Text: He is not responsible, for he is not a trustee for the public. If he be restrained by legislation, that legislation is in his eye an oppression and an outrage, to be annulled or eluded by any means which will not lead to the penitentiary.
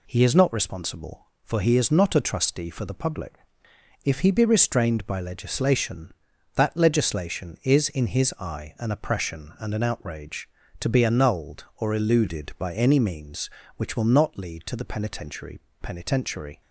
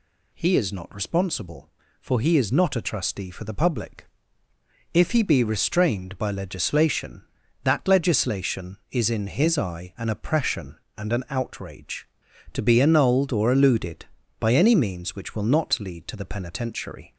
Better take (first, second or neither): second